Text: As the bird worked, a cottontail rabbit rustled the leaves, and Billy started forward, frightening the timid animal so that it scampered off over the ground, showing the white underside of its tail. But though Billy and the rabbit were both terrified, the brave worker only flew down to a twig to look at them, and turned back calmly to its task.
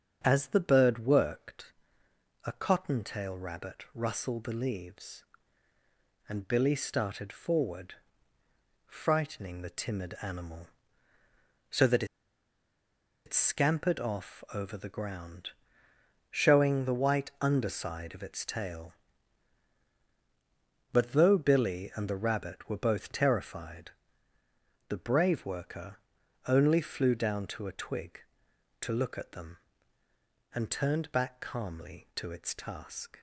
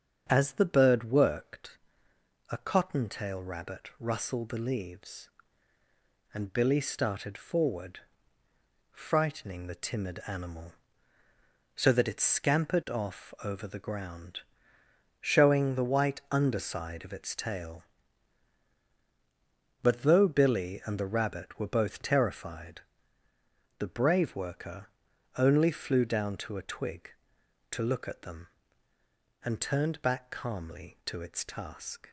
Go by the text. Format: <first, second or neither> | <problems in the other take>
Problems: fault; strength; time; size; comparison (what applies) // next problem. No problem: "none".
second | starts louder than the rest; strong; until 1.2 s; 7.5 dB; strong in the second // pauses between "that" and "it"; at 12.0 s; 1.2 s long // pauses between "worker" and "only"; noticeable; at 25.9 s; 0.50 s long; noticeable in the second